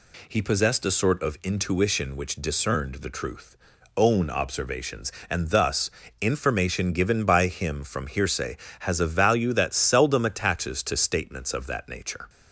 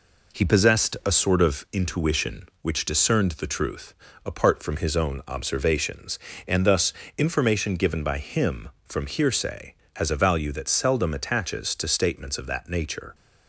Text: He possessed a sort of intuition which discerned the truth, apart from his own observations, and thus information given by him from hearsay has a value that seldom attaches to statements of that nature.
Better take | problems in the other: second | skips "apart from his"; at 3.7 s // pauses between "thus" and "information"; slight; at 5.8 s; 0.32 s long; slight in the second

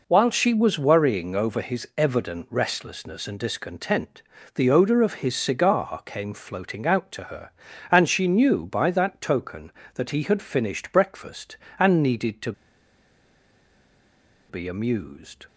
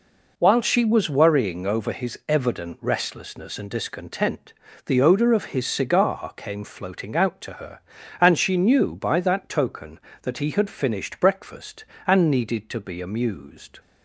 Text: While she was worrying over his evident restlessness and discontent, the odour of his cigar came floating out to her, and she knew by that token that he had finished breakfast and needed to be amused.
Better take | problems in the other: second | pauses between "to" and "be"; strong; at 12.5 s; 1.9 s long

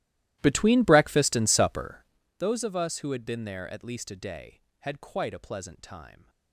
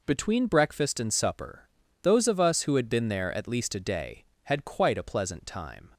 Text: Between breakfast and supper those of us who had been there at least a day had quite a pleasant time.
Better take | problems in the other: second | starts louder than the rest; strong; until 2.2 s; 15 dB // pauses between "supper" and "those"; slight; at 2.0 s; 0.34 s long; slight in the second

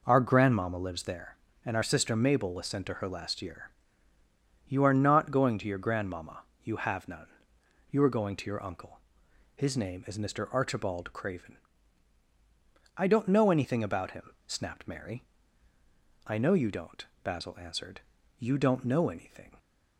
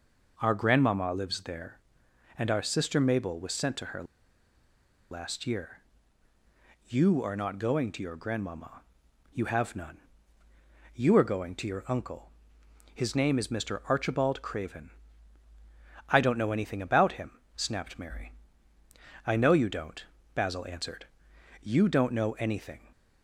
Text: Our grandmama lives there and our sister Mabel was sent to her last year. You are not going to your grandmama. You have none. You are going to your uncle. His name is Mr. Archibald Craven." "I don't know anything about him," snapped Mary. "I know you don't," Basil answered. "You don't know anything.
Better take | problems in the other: first | pauses between "her" and "last"; at 4.0 s; 1.0 s long

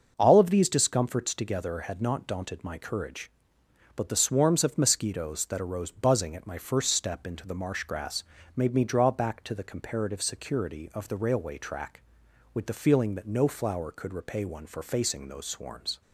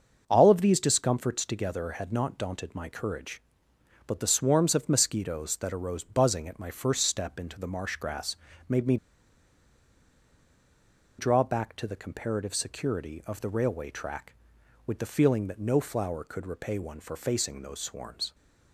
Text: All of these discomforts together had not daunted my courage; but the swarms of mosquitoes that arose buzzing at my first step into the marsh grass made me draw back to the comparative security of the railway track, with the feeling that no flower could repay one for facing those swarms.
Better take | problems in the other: first | starts louder than the rest; noticeable; until 1.2 s; 6 dB; noticeable in the first // pauses between "grass" and "made"; slight; at 8.3 s; 0.32 s long; slight in the first // pauses between "me" and "draw"; strong; at 8.9 s; 2.2 s long

